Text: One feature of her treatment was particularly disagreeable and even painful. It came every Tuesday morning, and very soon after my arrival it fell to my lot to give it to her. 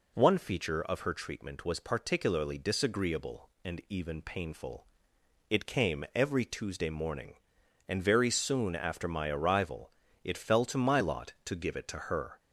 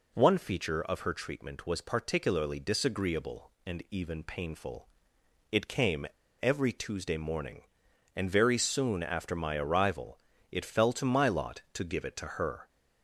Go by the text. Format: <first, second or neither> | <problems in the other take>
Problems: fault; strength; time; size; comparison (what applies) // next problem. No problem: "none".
first | pauses between "came" and "every"; slight; at 6.0 s; 0.35 s long // pauses between "arrival" and "it"; slight; at 10.2 s; 0.32 s long; slight in the first